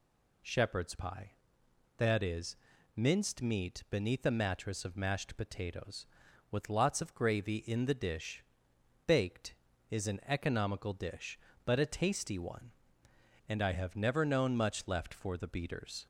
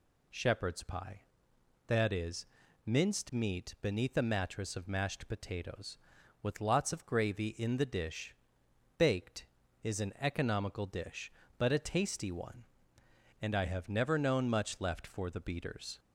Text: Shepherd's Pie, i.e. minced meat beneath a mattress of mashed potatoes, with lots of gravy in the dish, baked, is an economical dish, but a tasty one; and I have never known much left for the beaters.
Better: neither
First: none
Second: none

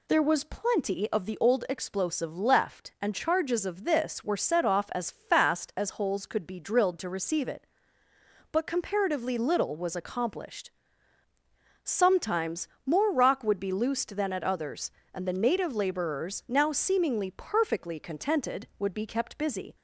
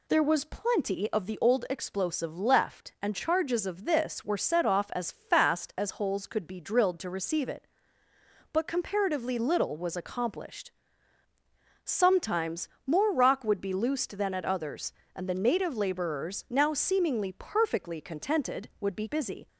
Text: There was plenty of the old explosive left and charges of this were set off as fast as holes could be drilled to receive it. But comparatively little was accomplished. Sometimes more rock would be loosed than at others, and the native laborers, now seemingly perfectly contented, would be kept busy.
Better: first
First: pauses between "Sometimes" and "more"; slight; at 12.6 s; 0.20 s long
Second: pauses between "Sometimes" and "more"; slight; at 12.6 s; 0.20 s long // skips "kept"; at 19.0 s

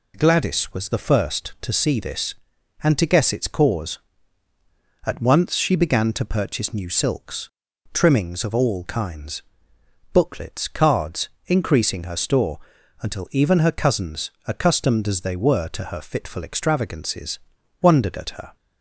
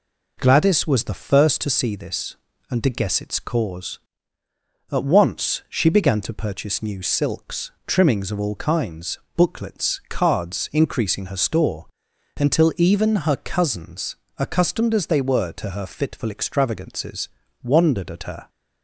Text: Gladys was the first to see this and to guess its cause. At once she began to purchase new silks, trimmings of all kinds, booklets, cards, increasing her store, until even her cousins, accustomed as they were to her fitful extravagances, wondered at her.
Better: neither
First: none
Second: none

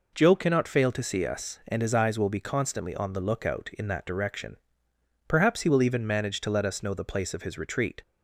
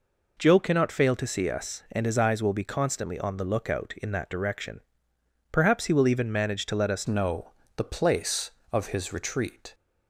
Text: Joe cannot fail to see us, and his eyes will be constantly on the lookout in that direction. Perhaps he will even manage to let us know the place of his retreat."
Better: first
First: none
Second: changes voice at "know"; from 7.0 s on; 2.7 s long // pauses between "know" and "the"; slight; at 7.5 s; 0.26 s long

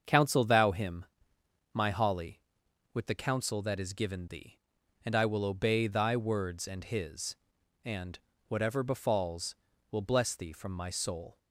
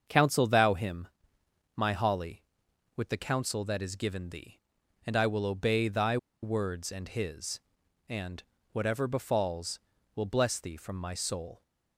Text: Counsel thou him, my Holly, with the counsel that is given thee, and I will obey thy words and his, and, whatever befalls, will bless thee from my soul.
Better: first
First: starts louder than the rest; until 1.7 s; 7 dB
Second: starts louder than the rest; until 1.7 s; 7 dB // pauses between "thy" and "words"; slight; at 6.1 s; 0.26 s long

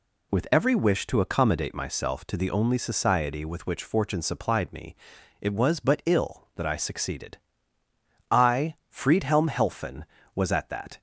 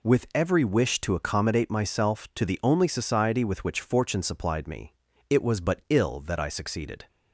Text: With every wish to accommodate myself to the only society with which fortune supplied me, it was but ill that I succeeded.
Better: second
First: goes on to say "I Friedhelm Helfen was at that"; strong; from 8.2 s on; 2.7 s long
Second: none

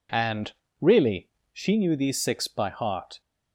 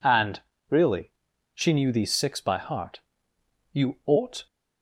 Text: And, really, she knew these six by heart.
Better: first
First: none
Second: goes on to say "You ought"; noticeable; from 3.7 s on; 0.74 s long

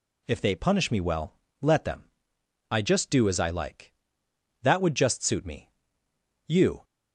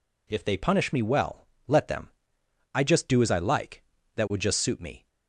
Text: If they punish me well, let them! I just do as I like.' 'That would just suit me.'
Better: second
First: goes on to say "You"; slight; from 6.4 s on; 0.38 s long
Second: none

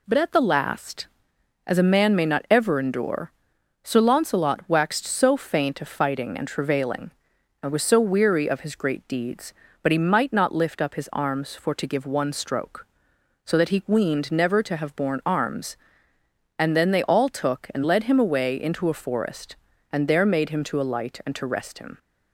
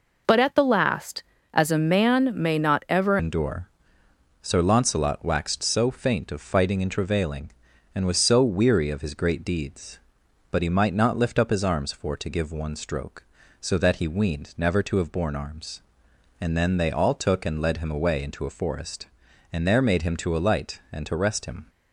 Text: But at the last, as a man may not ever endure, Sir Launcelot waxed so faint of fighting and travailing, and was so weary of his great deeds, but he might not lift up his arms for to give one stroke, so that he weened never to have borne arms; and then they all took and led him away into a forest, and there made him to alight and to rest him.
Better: first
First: none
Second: changes voice at "endure"; from 3.1 s on; 18.5 s long

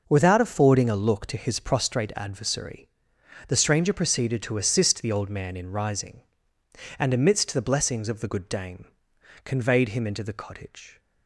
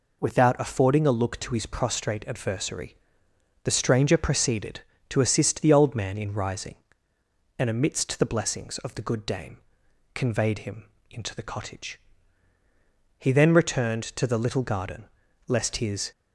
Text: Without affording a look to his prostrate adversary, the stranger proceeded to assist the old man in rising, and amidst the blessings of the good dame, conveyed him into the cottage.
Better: first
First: none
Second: pauses between "him" and "into"; slight; at 10.8 s; 0.26 s long // goes on to say "He then returned to the little garden lest his"; strong; from 13.1 s on; 2.9 s long

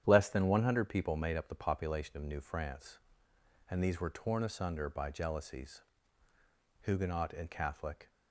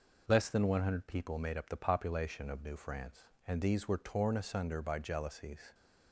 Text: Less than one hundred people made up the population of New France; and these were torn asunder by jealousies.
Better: second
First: starts louder than the rest; strong; until 1.0 s; 9.5 dB // goes on to say "Huguenot and Catholic"; noticeable; from 6.8 s on; 1.2 s long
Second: none

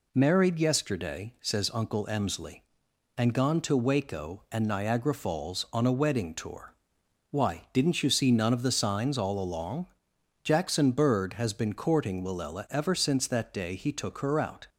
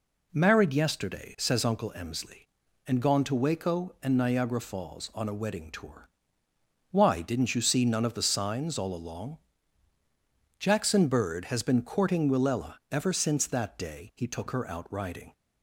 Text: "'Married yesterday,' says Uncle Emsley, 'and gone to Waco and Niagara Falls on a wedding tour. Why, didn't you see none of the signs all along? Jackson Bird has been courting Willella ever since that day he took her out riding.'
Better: second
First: stops before "riding"; at 14.6 s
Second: none

